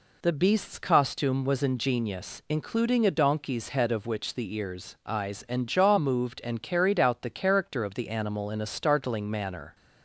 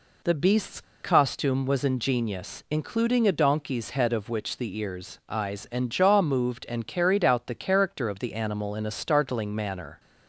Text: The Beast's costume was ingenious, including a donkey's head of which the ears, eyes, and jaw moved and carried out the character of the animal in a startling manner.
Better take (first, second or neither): first